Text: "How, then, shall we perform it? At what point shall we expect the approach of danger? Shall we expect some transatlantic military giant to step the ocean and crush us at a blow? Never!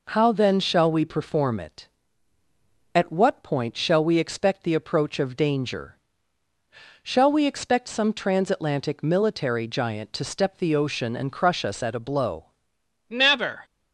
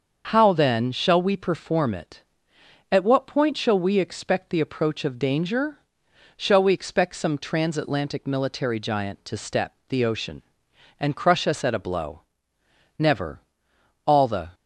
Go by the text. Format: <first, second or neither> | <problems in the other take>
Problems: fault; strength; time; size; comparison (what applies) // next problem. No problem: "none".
first | starts louder than the rest; until 1.3 s; 6.5 dB // goes on to say "All the"; slight; from 14.0 s on; 0.46 s long